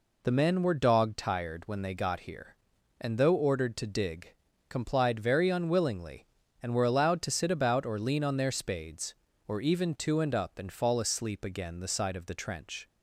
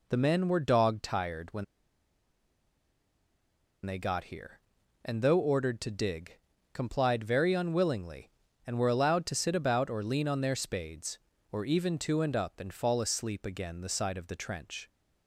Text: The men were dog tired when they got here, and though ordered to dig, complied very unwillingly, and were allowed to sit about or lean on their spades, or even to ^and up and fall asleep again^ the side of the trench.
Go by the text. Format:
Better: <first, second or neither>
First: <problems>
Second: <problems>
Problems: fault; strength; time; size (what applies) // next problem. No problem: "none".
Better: first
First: none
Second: pauses between "when" and "they"; strong; at 1.6 s; 2.2 s long